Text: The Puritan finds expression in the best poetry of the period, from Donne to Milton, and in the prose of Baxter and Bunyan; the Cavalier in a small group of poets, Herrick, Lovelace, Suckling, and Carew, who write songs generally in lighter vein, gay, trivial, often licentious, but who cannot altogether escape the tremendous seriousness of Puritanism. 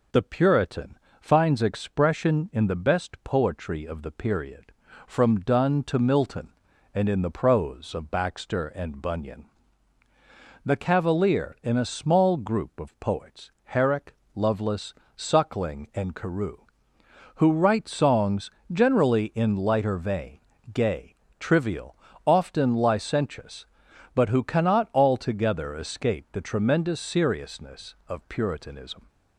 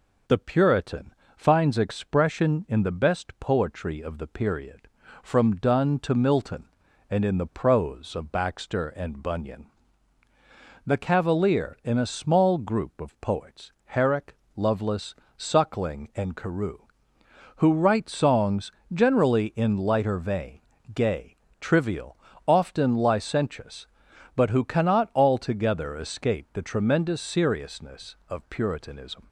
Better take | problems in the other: neither | pauses between "Puritan" and "finds"; slight; the same in both // pauses between "songs" and "generally"; slight; the same in both

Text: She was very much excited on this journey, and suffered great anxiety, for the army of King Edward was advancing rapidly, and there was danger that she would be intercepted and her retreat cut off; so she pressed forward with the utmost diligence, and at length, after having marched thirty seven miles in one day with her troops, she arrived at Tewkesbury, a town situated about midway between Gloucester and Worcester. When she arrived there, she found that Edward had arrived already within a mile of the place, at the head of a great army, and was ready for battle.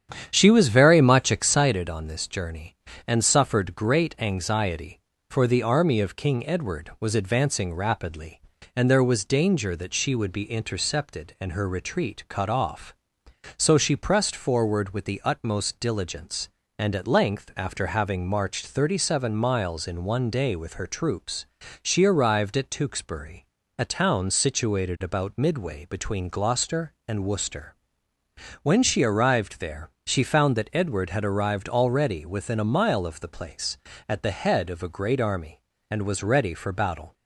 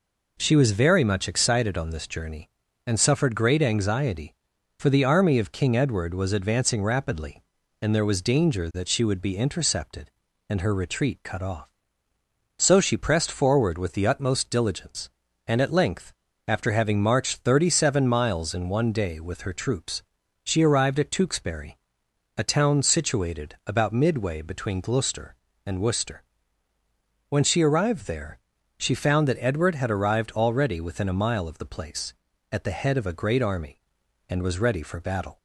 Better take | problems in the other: second | starts louder than the rest; strong; until 1.8 s; 9 dB

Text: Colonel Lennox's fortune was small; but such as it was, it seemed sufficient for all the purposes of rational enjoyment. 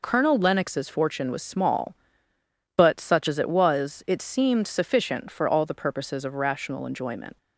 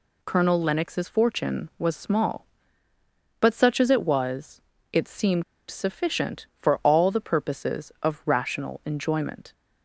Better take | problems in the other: first | pauses between "seemed" and "sufficient"; slight; at 5.4 s; 0.26 s long

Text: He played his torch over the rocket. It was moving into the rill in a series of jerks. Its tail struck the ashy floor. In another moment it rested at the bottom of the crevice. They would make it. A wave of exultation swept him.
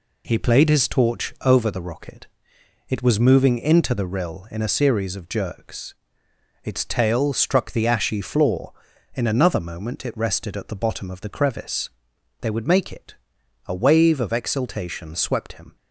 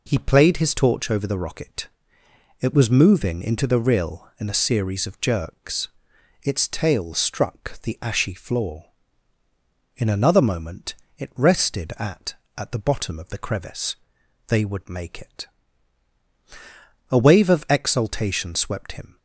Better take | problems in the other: first | pauses between "moment" and "it"; slight; at 10.9 s; 0.22 s long // says "at" twice; at 12.5 s

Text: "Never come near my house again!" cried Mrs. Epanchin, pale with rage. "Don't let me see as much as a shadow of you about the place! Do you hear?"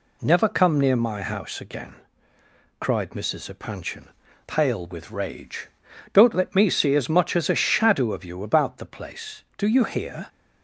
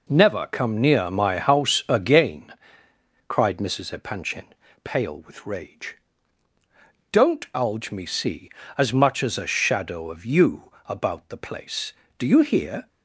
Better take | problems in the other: first | says "alge" for "let"; at 7.5 s

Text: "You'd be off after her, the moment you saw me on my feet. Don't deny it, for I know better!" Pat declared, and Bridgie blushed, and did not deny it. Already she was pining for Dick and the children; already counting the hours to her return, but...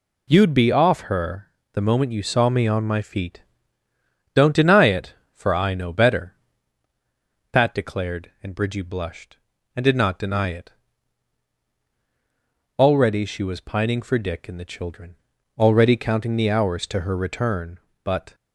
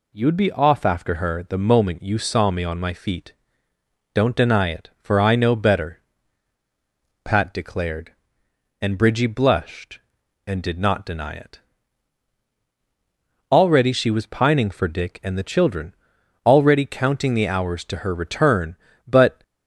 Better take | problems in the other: second | skips "after"; at 1.0 s

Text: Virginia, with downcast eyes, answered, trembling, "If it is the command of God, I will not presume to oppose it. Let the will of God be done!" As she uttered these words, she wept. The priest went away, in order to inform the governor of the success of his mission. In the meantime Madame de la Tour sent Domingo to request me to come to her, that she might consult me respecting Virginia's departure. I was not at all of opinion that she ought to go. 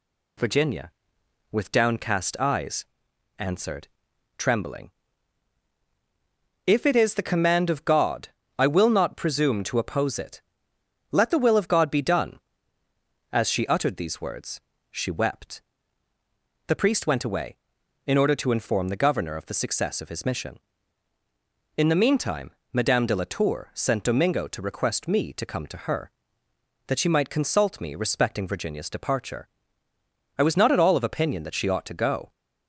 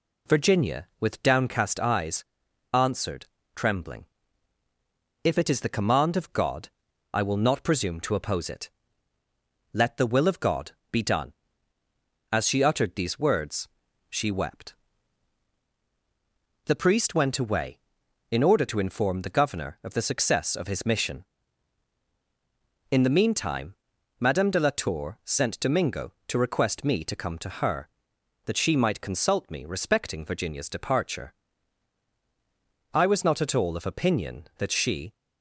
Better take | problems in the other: first | pauses between "God" and "be"; slight; at 10.7 s; 0.18 s long // pauses between "meantime" and "Madame"; at 23.7 s; 0.44 s long; slight in the first // stops before "ought to go"; at 35.1 s

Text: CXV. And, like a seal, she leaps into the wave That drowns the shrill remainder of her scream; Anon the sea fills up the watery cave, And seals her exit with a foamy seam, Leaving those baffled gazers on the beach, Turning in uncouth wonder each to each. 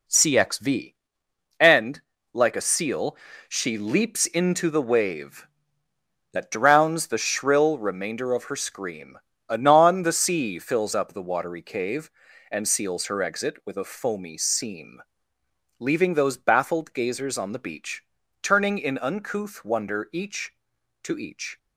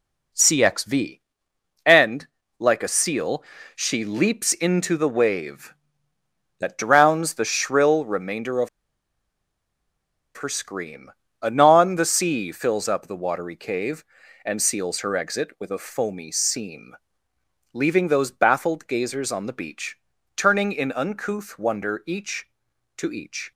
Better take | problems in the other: first | pauses between "of" and "her"; strong; at 8.6 s; 1.6 s long

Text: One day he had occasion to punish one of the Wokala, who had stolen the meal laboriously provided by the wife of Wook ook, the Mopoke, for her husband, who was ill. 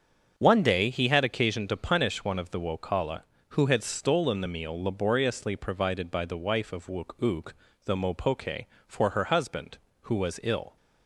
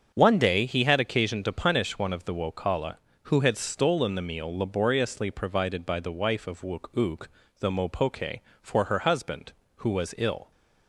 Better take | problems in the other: neither | starts louder than the rest; the same in both

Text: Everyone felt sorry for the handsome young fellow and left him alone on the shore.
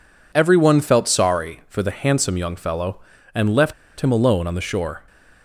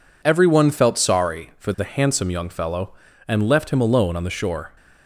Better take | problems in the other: second | pauses between "left" and "him"; slight; at 3.7 s; 0.26 s long

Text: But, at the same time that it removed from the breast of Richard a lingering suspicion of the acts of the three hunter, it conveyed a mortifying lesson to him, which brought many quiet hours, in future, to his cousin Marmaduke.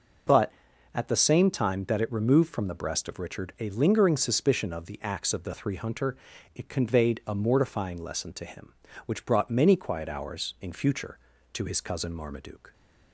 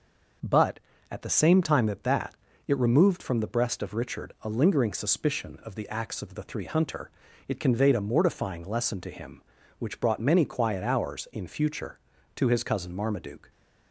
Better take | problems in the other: first | says "that" twice; at 2.0 s

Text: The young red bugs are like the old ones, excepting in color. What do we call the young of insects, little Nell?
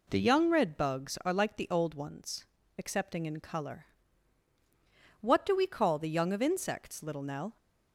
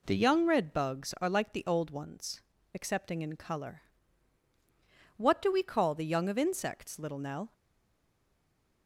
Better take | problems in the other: first | stays silent after the last word; noticeable; from 7.5 s on; 1.3 s long

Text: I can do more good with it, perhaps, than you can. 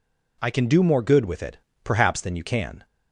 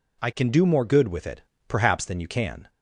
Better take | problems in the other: neither | none

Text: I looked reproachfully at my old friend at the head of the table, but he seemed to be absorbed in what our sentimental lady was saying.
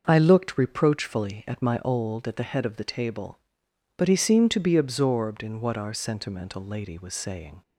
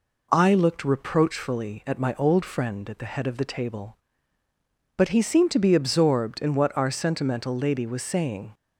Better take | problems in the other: second | starts louder than the rest; noticeable; until 1.0 s; 6 dB // skips "friend"; at 2.2 s

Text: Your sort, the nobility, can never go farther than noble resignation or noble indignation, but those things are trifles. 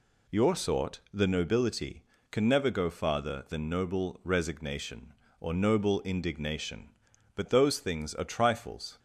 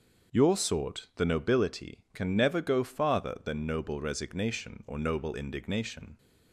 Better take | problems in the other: first | starts louder than the rest; until 1.4 s; 6.5 dB // stops before "but those things are trifles"; at 6.1 s

